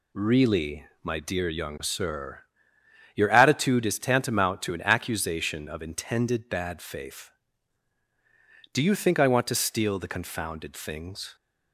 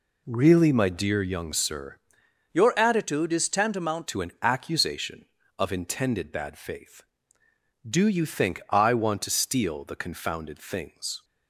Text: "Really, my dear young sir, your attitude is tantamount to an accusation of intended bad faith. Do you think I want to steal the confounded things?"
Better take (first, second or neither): first